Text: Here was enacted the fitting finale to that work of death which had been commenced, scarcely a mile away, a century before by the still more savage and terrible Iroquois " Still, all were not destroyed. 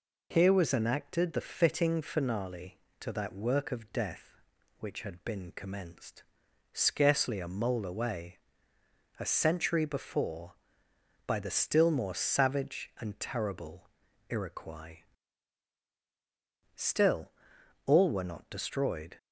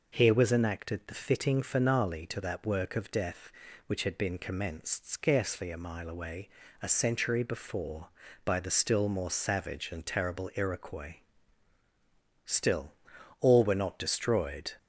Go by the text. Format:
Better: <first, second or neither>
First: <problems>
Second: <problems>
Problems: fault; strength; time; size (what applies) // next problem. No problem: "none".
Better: second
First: says "mole" for "mile"; at 7.4 s // pauses between "terrible" and "Iroquois"; at 13.8 s; 0.40 s long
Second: none